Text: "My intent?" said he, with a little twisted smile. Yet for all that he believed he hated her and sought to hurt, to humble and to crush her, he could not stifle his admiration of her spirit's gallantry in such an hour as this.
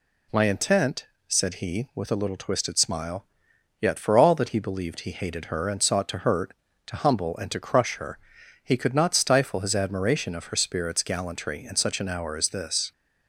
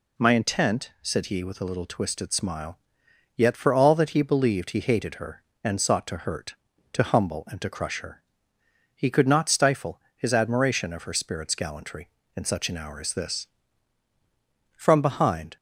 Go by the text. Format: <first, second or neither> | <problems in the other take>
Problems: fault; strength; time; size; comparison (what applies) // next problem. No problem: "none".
first | pauses between "stifle" and "his"; slight; at 10.0 s; 0.16 s long // goes on to say "From behind"; noticeable; from 14.7 s on; 0.80 s long